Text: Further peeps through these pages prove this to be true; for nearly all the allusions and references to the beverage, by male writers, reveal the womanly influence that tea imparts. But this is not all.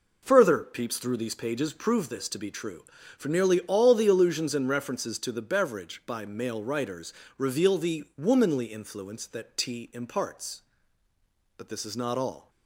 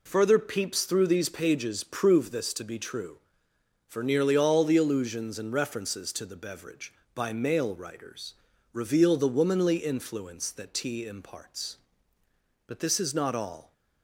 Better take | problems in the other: neither | none

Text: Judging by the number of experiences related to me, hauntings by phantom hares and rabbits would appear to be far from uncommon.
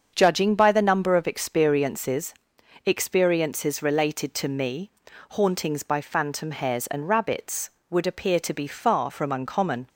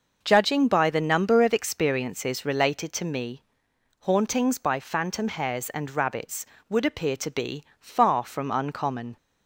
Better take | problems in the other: second | starts louder than the rest; until 1.1 s; 7 dB // says "experiences" twice; at 2.8 s

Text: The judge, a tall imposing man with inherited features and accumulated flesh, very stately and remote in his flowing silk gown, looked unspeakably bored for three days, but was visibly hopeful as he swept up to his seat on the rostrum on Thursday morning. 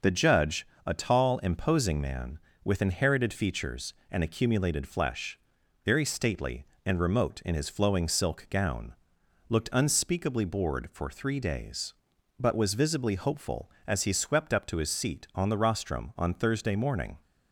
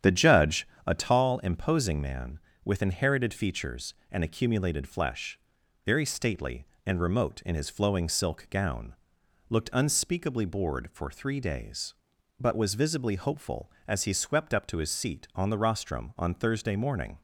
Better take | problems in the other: first | starts louder than the rest; strong; until 1.2 s; 9 dB

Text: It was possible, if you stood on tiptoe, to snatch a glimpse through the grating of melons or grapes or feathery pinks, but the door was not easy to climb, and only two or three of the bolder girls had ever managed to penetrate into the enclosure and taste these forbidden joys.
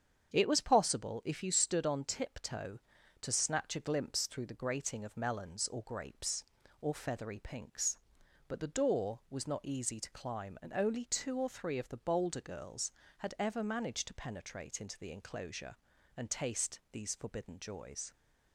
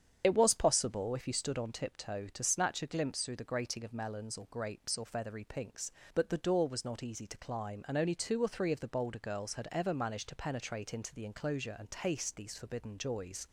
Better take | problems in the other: first | loses the start of "It"; at 0.2 s; 45 ms // starts louder than the rest; strong; until 1.2 s; 8 dB; strong in the first

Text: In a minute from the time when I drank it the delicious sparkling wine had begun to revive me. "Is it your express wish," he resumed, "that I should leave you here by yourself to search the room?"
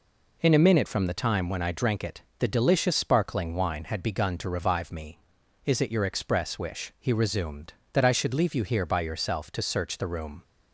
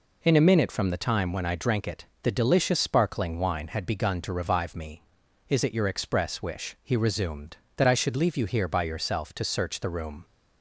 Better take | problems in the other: neither | pauses between "it" and "the"; slight; the same in both

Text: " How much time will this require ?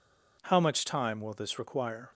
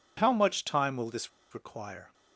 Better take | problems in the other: first | pauses between "this" and "require"; slight; at 1.2 s; 0.23 s long

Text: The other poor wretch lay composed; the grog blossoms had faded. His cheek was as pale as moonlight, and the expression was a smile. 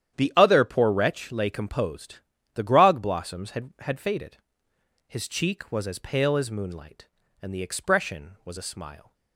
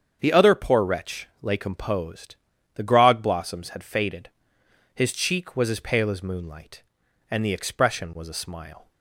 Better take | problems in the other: second | starts louder than the rest; strong; until 1.2 s; 10 dB; strong in the second // says "had" twice; at 3.7 s

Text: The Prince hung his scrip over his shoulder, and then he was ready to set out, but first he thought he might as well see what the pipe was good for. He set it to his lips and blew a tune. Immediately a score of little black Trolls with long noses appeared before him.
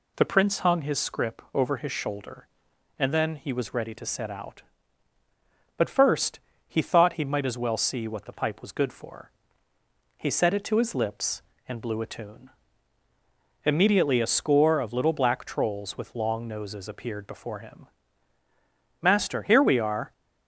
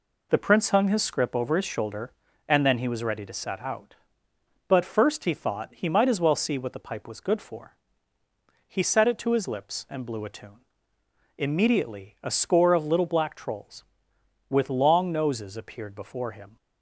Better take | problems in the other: second | pauses between "first" and "he"; slight; at 6.3 s; 0.30 s long // goes on to say "Master here we are"; noticeable; from 19.0 s on; 1.1 s long

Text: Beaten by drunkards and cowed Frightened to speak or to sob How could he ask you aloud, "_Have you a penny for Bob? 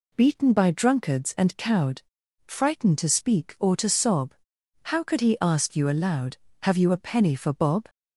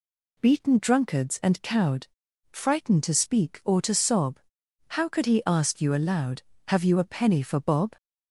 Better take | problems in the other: first | skips "by"; at 0.7 s // pauses between "cowed" and "Frightened"; at 2.0 s; 0.44 s long; also in the first // pauses between "sob" and "How"; noticeable; at 4.3 s; 0.50 s long; noticeable in the first

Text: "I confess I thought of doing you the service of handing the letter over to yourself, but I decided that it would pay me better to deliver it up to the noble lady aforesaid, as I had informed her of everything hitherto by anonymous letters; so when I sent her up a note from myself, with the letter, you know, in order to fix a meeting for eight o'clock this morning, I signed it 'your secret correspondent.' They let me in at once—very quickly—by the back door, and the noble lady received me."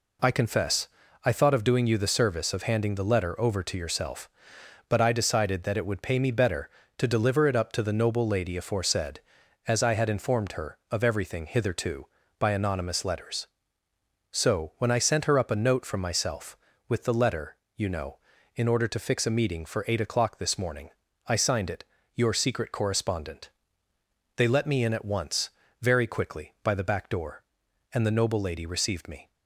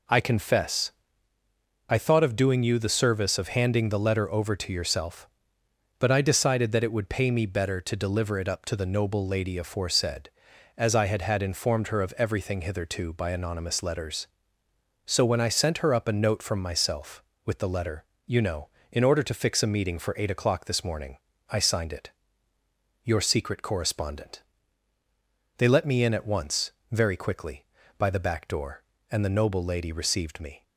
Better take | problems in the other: first | pauses between "confess" and "I"; noticeable; at 0.9 s; 0.98 s long; also in the first // says "had" twice; at 11.2 s // pauses between "it" and "your"; noticeable; at 22.1 s; 0.94 s long; slight in the first

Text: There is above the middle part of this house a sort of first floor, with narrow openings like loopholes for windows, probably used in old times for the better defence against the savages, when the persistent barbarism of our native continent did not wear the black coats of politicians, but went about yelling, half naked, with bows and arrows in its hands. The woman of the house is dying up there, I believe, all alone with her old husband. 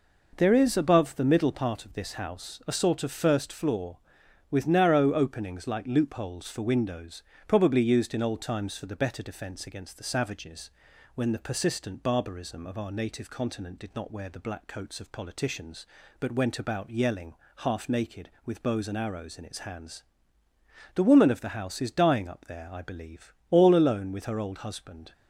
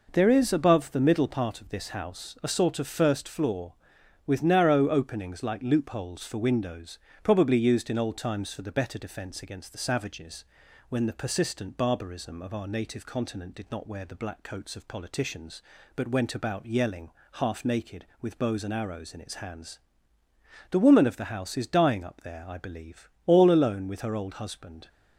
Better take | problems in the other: neither | none

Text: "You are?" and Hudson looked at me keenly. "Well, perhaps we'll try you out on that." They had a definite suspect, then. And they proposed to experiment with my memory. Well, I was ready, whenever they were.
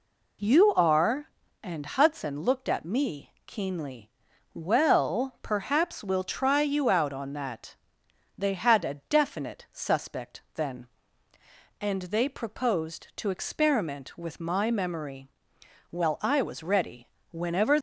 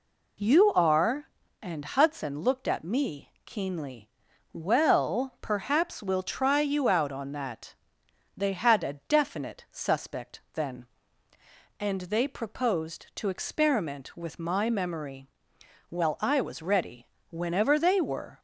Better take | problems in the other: second | pauses between "me" and "keenly"; slight; at 3.2 s; 0.16 s long; slight in the second // stops before "they were"; at 17.7 s

